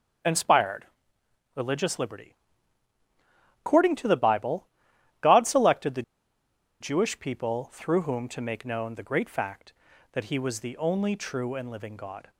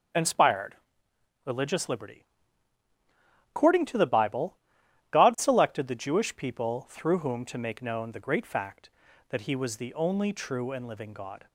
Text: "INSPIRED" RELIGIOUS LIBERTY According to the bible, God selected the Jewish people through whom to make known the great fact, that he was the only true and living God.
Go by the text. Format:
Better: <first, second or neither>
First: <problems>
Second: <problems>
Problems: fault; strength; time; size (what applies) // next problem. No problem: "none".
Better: second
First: starts louder than the rest; strong; until 1.9 s; 8 dB // pauses between "INSPIRED" and "RELIGIOUS"; noticeable; at 0.8 s; 0.70 s long // pauses between "LIBERTY" and "According"; strong; at 2.3 s; 1.2 s long // pauses between "the" and "Jewish"; noticeable; at 6.0 s; 0.78 s long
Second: starts louder than the rest; strong; until 1.8 s; 8 dB // pauses between "INSPIRED" and "RELIGIOUS"; noticeable; at 0.7 s; 0.70 s long // pauses between "LIBERTY" and "According"; strong; at 2.2 s; 1.2 s long